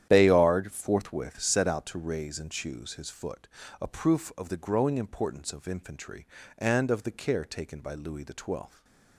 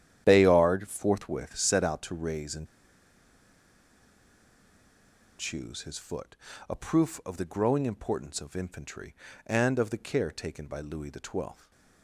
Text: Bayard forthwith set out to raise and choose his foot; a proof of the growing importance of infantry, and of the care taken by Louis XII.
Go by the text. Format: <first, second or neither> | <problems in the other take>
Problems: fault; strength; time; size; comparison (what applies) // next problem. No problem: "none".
first | starts louder than the rest; strong; until 1.2 s; 10.5 dB; strong in the first // pauses between "and" and "choose"; strong; at 2.6 s; 2.7 s long // stays silent after the last word; slight; from 11.5 s on; 0.5 s long; slight in the first